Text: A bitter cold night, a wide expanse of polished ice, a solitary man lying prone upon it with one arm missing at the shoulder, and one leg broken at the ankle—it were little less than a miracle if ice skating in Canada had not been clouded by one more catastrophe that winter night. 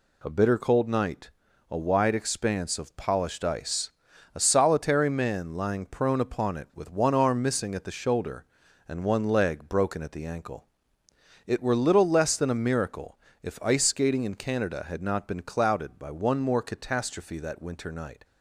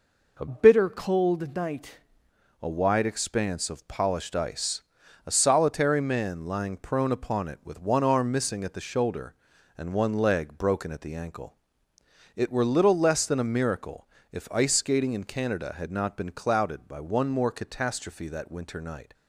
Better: first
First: pauses between "miracle" and "if"; slight; at 13.1 s; 0.24 s long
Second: changes voice from "bitter" to "night"; from 0.4 to 1.9 s; 1.5 s long // pauses between "miracle" and "if"; slight; at 14.0 s; 0.24 s long

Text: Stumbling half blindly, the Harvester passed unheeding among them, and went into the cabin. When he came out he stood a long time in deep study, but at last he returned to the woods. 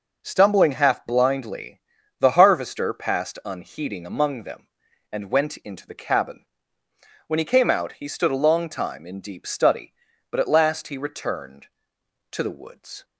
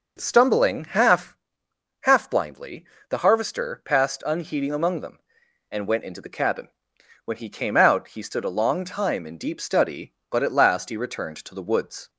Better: first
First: none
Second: says "half" twice; at 2.0 s

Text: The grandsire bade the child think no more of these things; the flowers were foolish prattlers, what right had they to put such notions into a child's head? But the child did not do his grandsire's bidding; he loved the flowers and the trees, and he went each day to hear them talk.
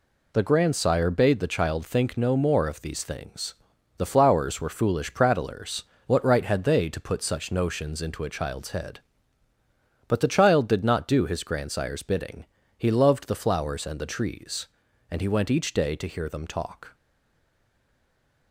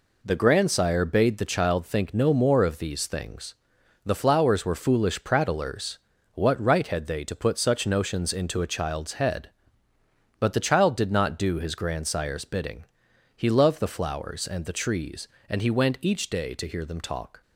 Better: second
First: stays silent after the last word; noticeable; from 16.9 s on; 1.6 s long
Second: none

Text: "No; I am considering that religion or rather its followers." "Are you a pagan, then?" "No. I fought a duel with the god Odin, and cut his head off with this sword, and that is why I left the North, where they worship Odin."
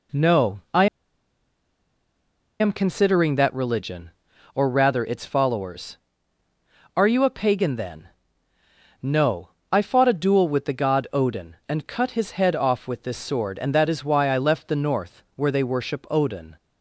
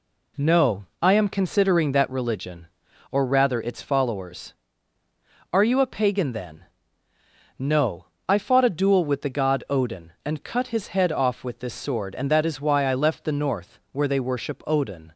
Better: second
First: pauses between "I" and "am"; strong; at 0.8 s; 1.7 s long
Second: none

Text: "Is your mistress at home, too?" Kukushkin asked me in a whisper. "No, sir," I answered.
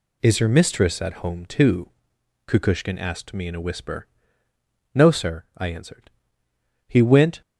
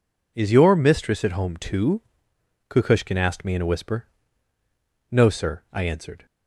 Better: second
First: goes on to say "He went"; from 6.8 s on; 0.54 s long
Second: none

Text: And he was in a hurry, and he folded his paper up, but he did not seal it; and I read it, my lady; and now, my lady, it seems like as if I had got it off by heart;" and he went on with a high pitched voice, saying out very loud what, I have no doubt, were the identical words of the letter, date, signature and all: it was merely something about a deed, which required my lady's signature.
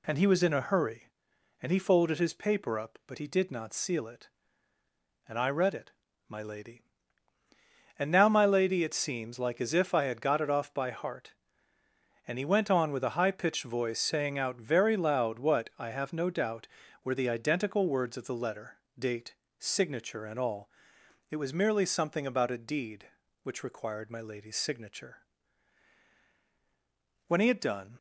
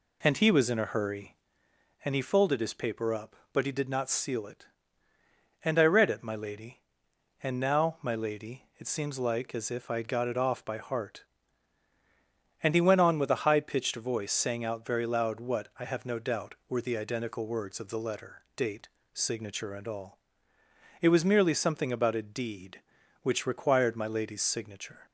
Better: second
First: goes on to say "When he had done"; noticeable; from 27.2 s on; 0.70 s long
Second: none

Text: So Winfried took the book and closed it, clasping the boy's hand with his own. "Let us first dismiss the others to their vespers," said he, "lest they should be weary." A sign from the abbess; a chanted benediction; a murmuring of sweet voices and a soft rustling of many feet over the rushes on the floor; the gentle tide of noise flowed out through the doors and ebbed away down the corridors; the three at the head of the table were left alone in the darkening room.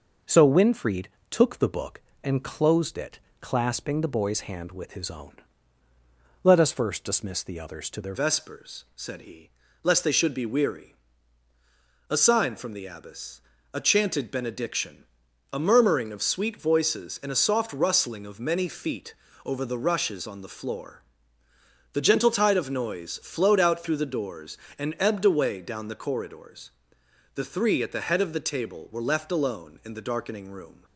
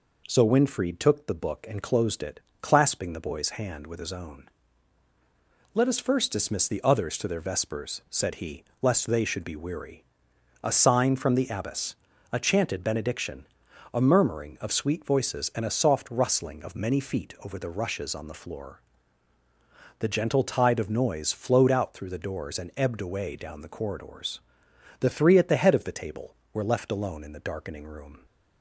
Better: second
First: pauses between "Winfried" and "took"; slight; at 1.0 s; 0.22 s long // changes voice at "vespers"; from 8.1 s on; 22.7 s long // pauses between "feet" and "over"; slight; at 19.1 s; 0.28 s long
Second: none

